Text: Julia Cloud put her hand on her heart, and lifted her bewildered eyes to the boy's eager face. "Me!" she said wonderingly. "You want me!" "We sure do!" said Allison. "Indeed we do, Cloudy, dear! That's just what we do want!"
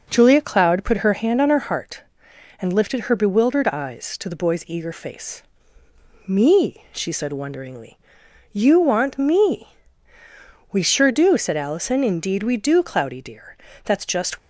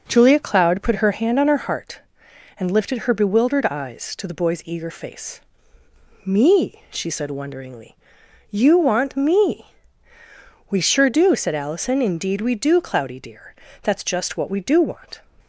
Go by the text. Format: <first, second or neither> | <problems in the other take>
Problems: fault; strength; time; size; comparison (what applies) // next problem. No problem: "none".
second | stops before "what we do want"; at 14.3 s